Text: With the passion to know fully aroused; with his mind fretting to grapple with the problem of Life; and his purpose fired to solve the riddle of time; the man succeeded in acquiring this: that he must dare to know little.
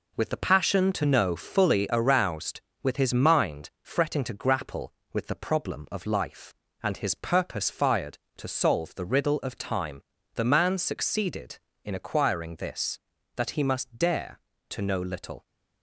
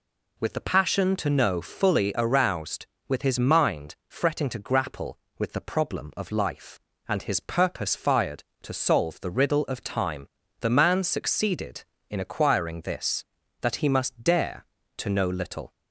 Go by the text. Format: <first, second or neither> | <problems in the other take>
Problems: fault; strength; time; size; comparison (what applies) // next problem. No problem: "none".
second | gets quieter; throughout; 7 dB